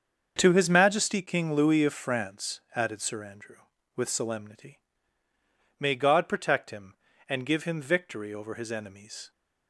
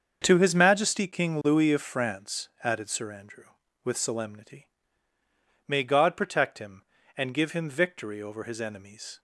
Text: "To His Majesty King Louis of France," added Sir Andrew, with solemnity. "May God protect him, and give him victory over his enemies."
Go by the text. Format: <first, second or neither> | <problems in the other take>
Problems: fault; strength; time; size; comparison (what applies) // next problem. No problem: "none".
neither | starts louder than the rest; the same in both